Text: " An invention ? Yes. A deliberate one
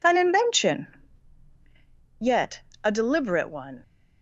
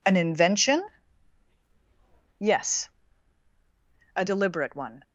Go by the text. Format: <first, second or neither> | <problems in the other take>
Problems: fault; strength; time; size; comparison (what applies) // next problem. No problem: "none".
second | says "Yet" for "Yes"; at 2.2 s